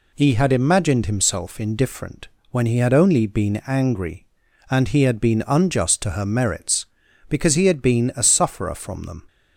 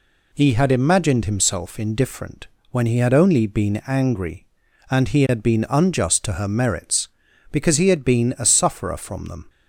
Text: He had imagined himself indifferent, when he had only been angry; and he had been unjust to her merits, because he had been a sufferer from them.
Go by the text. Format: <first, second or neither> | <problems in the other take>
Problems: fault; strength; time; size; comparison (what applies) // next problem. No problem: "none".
neither | none